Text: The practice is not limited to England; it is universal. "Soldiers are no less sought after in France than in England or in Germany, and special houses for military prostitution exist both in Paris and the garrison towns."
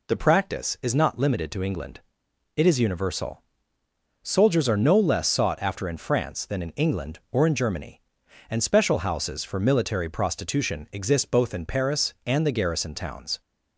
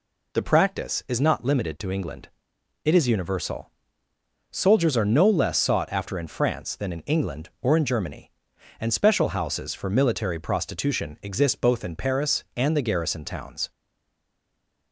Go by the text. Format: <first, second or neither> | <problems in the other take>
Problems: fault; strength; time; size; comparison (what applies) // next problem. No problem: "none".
first | stays silent after the last word; noticeable; from 13.7 s on; 1.2 s long